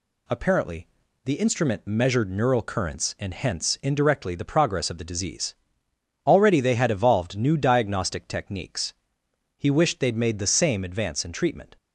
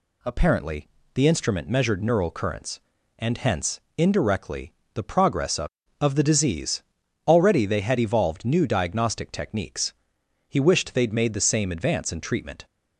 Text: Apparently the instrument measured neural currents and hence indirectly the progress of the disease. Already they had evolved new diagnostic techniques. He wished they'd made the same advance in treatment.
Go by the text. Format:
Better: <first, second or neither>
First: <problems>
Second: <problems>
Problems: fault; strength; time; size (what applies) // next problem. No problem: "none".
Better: first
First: pauses between "Apparently" and "the"; slight; at 0.8 s; 0.36 s long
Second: pauses between "Apparently" and "the"; slight; at 0.8 s; 0.28 s long // pauses between "hence" and "indirectly"; slight; at 3.7 s; 0.18 s long // pauses between "indirectly" and "the"; slight; at 4.7 s; 0.20 s long // says "of" twice; at 5.9 s